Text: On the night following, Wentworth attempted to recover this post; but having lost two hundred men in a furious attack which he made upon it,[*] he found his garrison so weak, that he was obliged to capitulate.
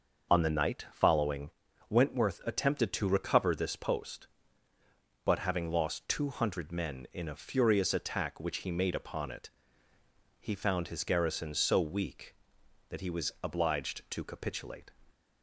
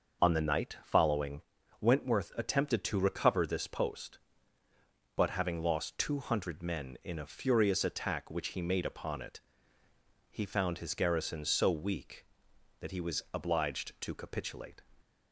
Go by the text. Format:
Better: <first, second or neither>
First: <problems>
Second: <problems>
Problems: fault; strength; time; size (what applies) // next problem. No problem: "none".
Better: neither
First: starts louder than the rest; until 1.3 s; 6 dB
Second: starts louder than the rest; until 1.3 s; 6 dB